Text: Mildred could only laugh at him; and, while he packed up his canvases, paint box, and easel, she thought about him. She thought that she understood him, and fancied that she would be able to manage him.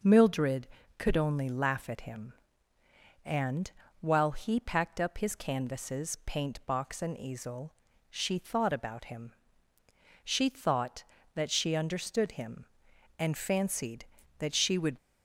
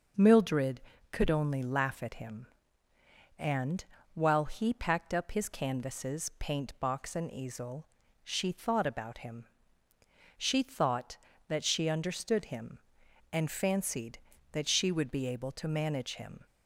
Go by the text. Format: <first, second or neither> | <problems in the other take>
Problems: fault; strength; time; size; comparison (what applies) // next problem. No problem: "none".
second | stops before "be able to manage him"; at 14.9 s